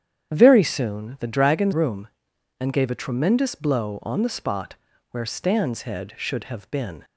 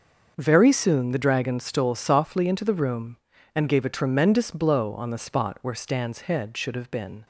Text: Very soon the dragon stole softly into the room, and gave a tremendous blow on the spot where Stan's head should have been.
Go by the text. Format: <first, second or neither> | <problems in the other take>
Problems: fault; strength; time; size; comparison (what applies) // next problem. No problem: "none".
second | starts louder than the rest; strong; until 1.3 s; 9 dB; also in the second // skips "stole softly into the"; at 1.7 s // pauses between "spot" and "where"; at 4.7 s; 0.38 s long